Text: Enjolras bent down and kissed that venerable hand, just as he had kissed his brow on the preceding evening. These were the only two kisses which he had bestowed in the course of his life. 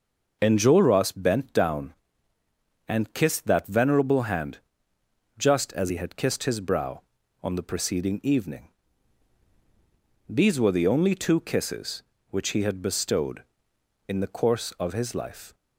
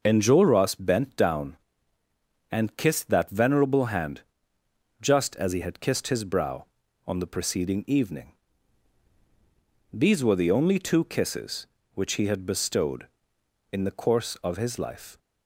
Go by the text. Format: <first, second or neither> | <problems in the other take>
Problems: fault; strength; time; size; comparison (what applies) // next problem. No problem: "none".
neither | none